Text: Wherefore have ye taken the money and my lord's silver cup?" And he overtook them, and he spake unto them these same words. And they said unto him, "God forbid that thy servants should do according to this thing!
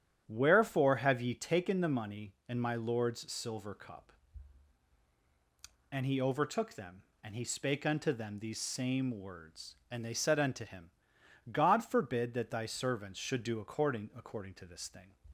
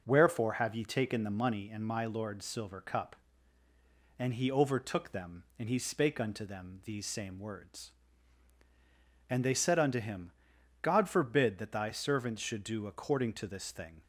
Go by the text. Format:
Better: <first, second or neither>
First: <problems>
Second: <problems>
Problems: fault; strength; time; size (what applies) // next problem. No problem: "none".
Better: second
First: starts louder than the rest; strong; until 1.2 s; 9.5 dB // says "according" twice; at 14.1 s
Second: none